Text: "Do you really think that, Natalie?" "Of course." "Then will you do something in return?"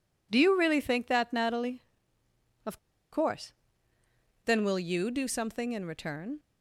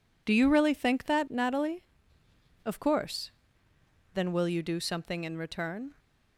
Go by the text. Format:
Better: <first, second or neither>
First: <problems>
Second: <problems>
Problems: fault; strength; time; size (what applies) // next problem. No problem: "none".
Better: second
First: pauses between "Of" and "course"; slight; at 2.7 s; 0.34 s long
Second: none